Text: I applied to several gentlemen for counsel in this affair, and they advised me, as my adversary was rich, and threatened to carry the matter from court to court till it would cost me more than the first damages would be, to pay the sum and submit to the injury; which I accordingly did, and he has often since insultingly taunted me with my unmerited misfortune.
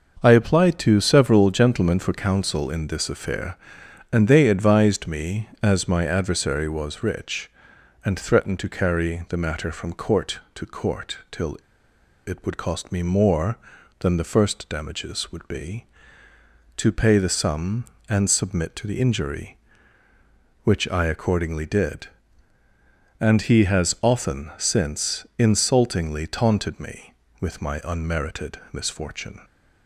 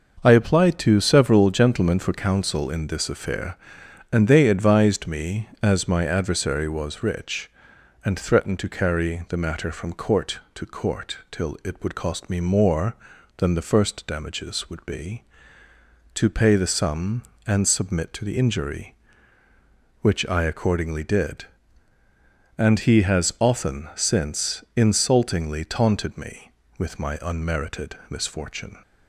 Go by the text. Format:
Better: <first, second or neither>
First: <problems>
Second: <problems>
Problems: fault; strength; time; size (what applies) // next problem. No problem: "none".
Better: second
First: starts louder than the rest; noticeable; until 1.2 s; 6 dB // pauses between "till" and "it"; noticeable; at 11.5 s; 0.70 s long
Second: none